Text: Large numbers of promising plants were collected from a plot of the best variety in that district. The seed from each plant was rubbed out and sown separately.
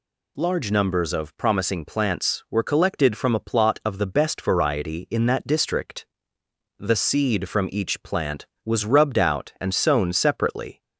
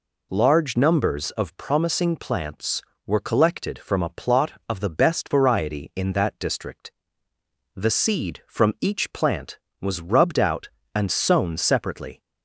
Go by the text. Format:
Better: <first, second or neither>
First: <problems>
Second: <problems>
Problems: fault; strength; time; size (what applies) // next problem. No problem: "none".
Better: neither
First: none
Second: none